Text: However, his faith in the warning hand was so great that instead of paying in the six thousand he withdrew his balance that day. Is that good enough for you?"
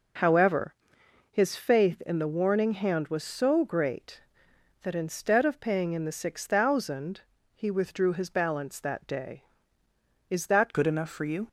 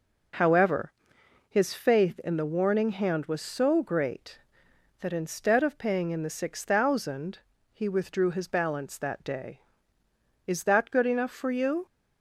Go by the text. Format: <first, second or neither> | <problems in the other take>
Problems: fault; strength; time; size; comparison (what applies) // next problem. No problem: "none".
second | pauses between "thousand" and "he"; slight; at 7.2 s; 0.34 s long; slight in the second // changes voice at "good"; from 10.7 s on; 0.7 s long